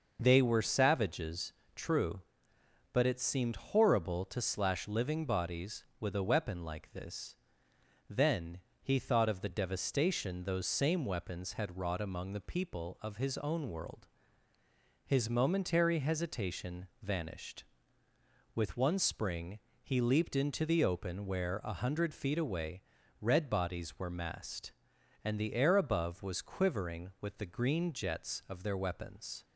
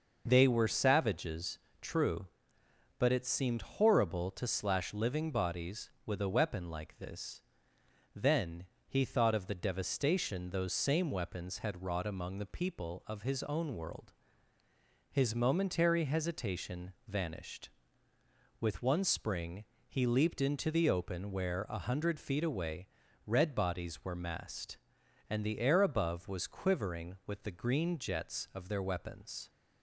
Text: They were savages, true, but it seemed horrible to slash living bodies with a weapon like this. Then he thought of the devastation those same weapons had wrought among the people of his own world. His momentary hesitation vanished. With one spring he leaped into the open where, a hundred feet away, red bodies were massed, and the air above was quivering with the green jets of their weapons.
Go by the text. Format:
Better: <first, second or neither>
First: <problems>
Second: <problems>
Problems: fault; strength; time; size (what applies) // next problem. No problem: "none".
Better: neither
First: pauses between "Then" and "he"; slight; at 8.5 s; 0.24 s long // pauses between "spring" and "he"; slight; at 19.5 s; 0.24 s long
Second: pauses between "Then" and "he"; slight; at 8.6 s; 0.24 s long // pauses between "spring" and "he"; slight; at 19.6 s; 0.24 s long